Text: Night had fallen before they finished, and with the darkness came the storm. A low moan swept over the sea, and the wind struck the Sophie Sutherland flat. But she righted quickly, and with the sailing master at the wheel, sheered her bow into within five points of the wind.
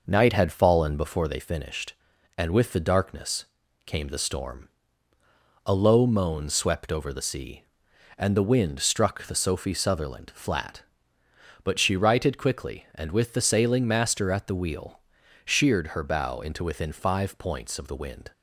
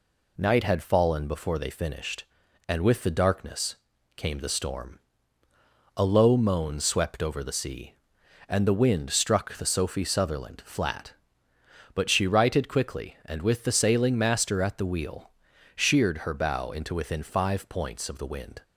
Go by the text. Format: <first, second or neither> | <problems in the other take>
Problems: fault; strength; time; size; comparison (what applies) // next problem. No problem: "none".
second | starts louder than the rest; noticeable; until 1.4 s; 5.5 dB // pauses between "darkness" and "came"; at 3.4 s; 0.42 s long; also in the second